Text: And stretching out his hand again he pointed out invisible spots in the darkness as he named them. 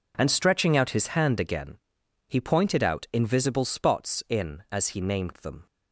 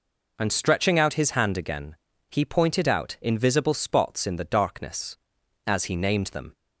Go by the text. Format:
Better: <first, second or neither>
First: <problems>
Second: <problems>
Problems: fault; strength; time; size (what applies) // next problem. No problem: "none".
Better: second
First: pauses between "again" and "he"; noticeable; at 1.7 s; 0.50 s long // skips "the darkness"; at 4.6 s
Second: pauses between "again" and "he"; slight; at 1.9 s; 0.34 s long